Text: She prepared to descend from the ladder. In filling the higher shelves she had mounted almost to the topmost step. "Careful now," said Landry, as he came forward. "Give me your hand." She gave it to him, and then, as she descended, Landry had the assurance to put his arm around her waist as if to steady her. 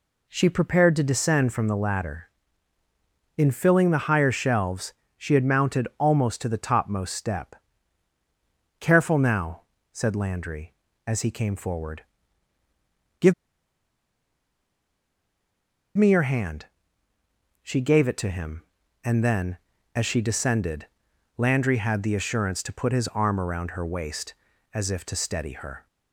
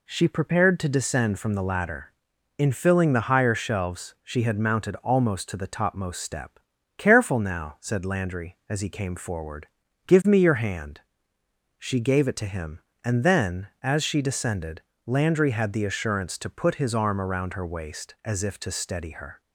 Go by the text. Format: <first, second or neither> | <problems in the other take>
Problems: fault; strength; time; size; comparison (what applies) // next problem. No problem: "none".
second | pauses between "shelves" and "she"; slight; at 4.9 s; 0.24 s long // pauses between "Give" and "me"; strong; at 13.3 s; 2.6 s long